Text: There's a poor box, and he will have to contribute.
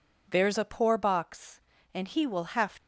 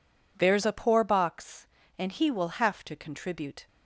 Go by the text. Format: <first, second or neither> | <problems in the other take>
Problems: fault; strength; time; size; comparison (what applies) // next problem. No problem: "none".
second | stops before "to contribute"; at 2.7 s